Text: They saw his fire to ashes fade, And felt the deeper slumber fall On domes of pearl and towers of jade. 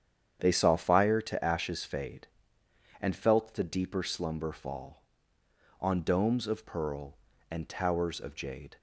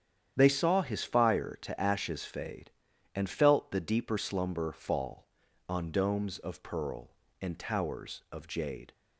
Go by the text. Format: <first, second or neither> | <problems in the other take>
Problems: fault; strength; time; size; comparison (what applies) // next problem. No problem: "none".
second | starts louder than the rest; strong; until 1.4 s; 8.5 dB; strong in the second // skips "his"; at 0.7 s